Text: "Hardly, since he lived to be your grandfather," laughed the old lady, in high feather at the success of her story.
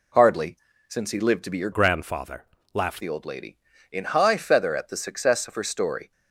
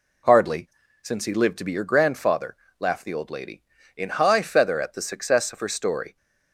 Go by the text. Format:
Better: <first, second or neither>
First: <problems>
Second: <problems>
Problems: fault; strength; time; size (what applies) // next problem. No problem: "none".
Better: second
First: changes voice from "grandfather" to "laughed"; from 1.7 to 3.0 s; 1.3 s long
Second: none